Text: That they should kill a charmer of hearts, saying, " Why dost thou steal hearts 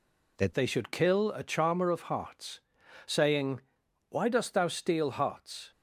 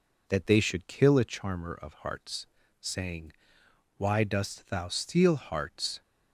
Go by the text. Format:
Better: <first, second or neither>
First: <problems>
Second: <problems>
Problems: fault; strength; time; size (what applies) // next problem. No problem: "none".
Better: second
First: changes voice at "they"; from 0.5 s on; 5.2 s long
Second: none